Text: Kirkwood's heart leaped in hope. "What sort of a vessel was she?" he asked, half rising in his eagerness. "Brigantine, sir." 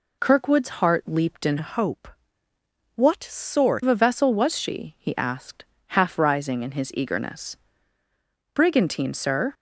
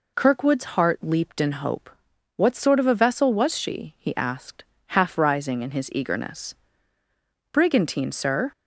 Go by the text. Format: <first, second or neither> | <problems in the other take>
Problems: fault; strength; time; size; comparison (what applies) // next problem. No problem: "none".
second | changes voice from "hope" to "sort"; from 1.5 to 3.8 s; 2.3 s long